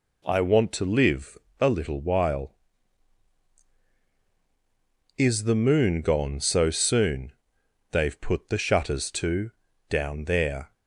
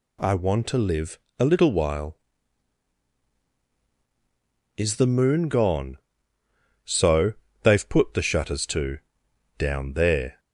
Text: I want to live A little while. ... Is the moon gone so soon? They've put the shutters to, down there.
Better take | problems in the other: first | pauses between "live" and "A"; slight; at 1.1 s; 0.22 s long; slight in the first // skips "soon"; at 7.4 s

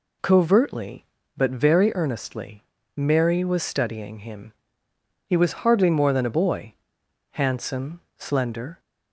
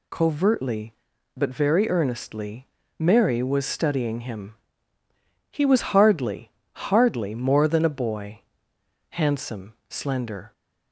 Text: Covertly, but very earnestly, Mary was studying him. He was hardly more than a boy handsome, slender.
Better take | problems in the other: first | says "hardly" twice; at 6.9 s // pauses between "boy" and "handsome"; noticeable; at 8.4 s; 0.70 s long; noticeable in the first

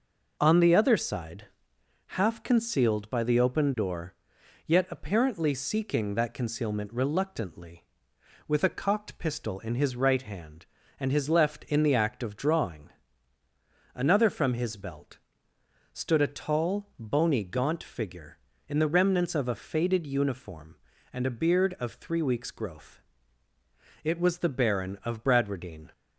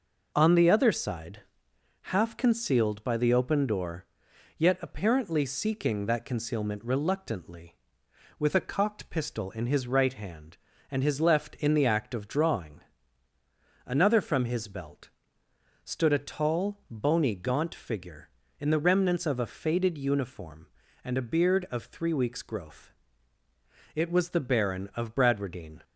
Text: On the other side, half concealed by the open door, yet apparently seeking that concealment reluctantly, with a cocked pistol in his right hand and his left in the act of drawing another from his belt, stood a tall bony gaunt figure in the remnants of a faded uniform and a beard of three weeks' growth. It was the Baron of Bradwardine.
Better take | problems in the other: neither | pauses between "drawing" and "another"; the same in both

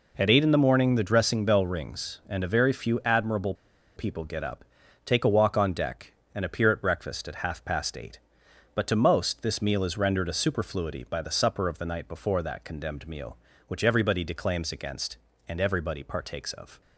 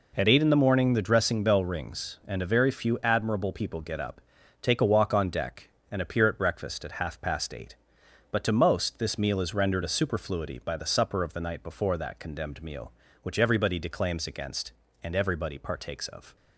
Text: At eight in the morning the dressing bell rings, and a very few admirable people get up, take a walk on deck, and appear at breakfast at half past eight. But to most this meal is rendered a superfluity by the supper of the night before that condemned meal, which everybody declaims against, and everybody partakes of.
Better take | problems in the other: second | pauses between "admirable" and "people"; at 3.5 s; 0.42 s long

